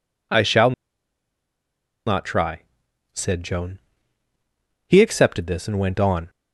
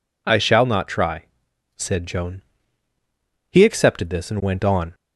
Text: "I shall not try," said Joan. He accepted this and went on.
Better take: second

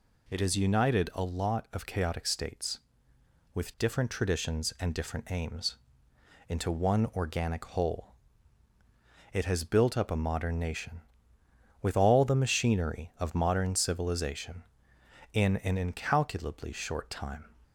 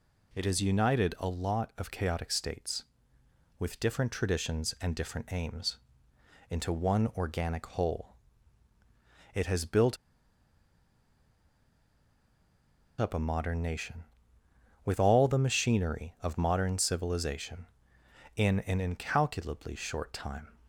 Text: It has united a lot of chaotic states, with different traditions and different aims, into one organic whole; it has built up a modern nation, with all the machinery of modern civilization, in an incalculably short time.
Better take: first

